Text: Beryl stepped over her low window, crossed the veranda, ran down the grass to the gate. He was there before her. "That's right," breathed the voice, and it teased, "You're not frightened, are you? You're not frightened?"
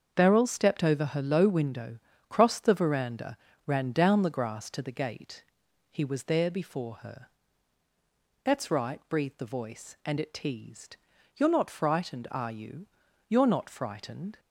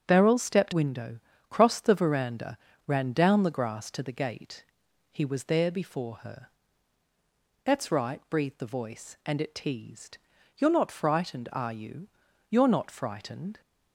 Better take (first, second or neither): first